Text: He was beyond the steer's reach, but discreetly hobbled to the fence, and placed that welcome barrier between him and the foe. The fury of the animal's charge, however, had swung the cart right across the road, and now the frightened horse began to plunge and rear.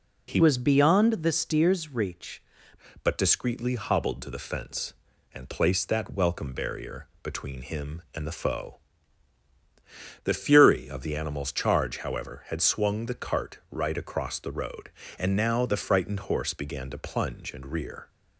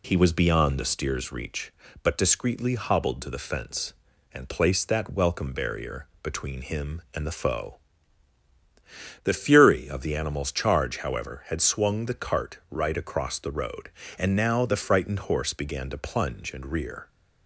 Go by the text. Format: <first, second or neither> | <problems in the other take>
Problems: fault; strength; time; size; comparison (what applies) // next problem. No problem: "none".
second | changes voice from "was" to "reach"; from 0.4 to 2.4 s; 2.0 s long // pauses between "barrier" and "between"; slight; at 7.0 s; 0.16 s long; slight in the second